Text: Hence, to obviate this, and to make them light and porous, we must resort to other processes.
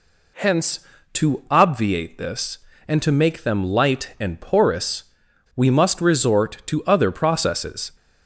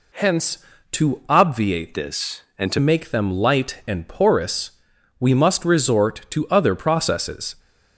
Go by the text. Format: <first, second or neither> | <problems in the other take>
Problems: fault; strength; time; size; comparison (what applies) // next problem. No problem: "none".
first | changes voice from "this" to "to"; from 1.9 to 2.7 s; 0.8 s long